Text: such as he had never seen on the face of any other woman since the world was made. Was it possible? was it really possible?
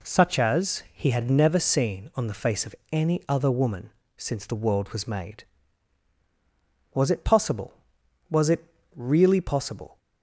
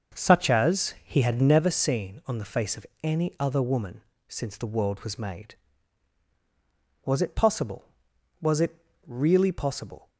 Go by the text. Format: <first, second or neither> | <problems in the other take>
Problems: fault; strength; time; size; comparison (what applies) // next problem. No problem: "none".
first | starts louder than the rest; noticeable; until 1.7 s; 6 dB // pauses between "of" and "any"; slight; at 2.8 s; 0.16 s long; slight in the first // pauses between "woman" and "since"; slight; at 4.0 s; 0.26 s long; slight in the first // pauses between "it" and "really"; slight; at 8.7 s; 0.30 s long; slight in the first